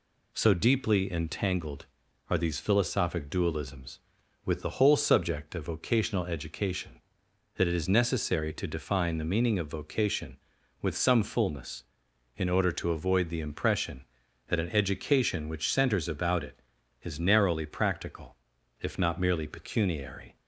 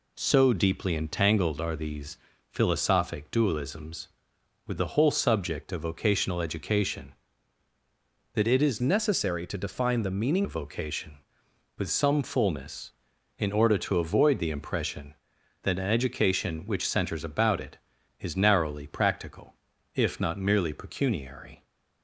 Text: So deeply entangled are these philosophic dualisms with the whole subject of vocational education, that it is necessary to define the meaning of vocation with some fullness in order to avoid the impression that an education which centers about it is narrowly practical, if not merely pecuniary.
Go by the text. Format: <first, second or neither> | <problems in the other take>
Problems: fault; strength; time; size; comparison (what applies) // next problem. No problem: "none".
first | pauses between "these" and "philosophic"; slight; at 2.1 s; 0.32 s long // changes voice from "necessary" to "meaning"; from 8.8 to 10.4 s; 1.6 s long